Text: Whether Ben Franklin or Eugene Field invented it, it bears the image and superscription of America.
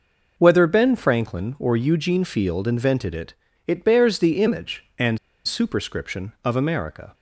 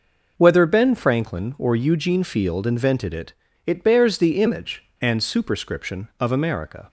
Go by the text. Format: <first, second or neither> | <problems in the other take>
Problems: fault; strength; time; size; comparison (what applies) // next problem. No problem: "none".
second | pauses between "and" and "superscription"; slight; at 5.1 s; 0.27 s long